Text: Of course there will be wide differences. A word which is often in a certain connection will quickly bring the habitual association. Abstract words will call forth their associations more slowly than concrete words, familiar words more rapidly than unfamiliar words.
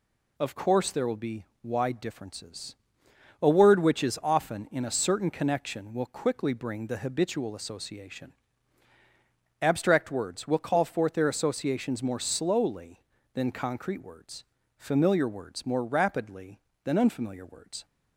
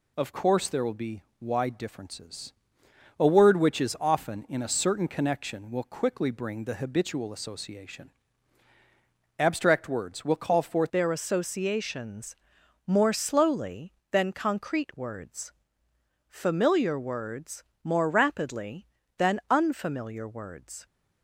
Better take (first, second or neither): first